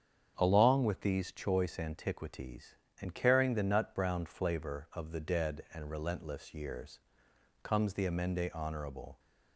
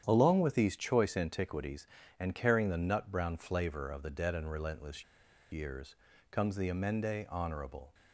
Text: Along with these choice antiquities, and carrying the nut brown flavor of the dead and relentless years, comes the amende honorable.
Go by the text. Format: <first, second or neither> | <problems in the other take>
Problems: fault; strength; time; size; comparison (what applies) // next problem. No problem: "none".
first | starts louder than the rest; strong; until 1.0 s; 9 dB; strong in the first // pauses between "relentless" and "years"; noticeable; at 5.0 s; 0.49 s long